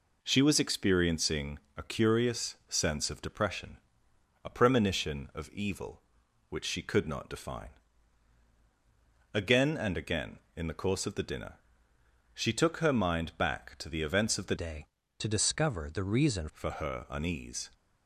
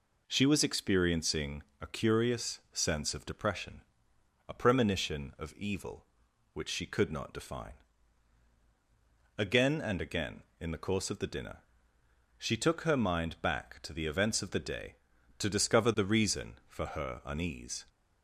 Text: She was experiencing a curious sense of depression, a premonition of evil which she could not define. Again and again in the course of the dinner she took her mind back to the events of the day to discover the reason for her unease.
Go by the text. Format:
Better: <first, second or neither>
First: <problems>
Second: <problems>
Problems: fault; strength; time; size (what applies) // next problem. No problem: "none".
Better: second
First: pauses between "experiencing" and "a"; slight; at 1.5 s; 0.18 s long // pauses between "dinner" and "she"; noticeable; at 11.5 s; 0.80 s long // changes voice from "day" to "reason"; from 14.5 to 16.4 s; 1.9 s long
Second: pauses between "experiencing" and "a"; slight; at 1.6 s; 0.18 s long // pauses between "dinner" and "she"; noticeable; at 11.5 s; 0.80 s long